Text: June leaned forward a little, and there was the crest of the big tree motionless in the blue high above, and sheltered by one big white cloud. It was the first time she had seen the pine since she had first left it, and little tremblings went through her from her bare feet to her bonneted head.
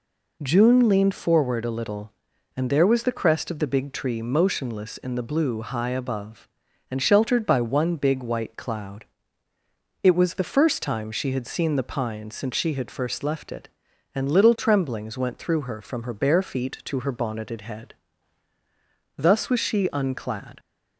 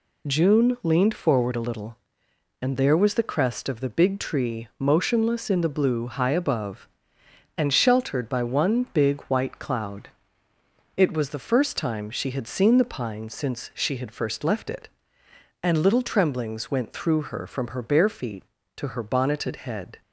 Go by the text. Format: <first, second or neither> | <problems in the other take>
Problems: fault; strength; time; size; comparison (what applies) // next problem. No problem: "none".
second | goes on to say "Thus was she unclad"; from 19.1 s on; 1.4 s long